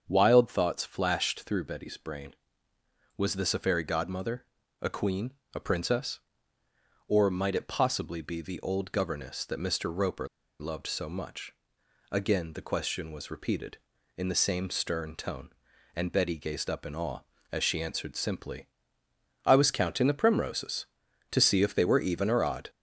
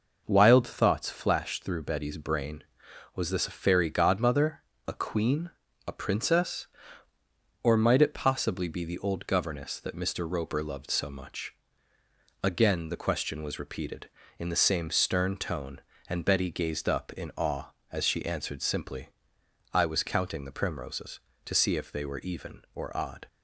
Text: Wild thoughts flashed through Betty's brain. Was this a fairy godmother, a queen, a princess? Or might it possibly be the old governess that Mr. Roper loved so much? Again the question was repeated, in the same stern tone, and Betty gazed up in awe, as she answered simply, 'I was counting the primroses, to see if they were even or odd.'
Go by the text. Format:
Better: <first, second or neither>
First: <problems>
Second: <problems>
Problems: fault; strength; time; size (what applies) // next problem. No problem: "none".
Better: second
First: starts louder than the rest; until 1.0 s; 7 dB // pauses between "Roper" and "loved"; slight; at 10.2 s; 0.31 s long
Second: none